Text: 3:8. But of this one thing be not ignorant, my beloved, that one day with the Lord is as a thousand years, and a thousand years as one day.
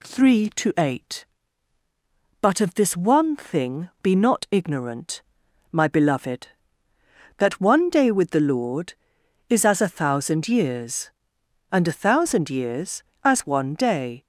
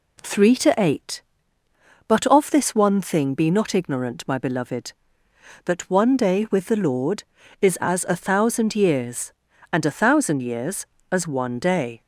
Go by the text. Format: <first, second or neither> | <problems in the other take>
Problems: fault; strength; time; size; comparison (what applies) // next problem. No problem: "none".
neither | none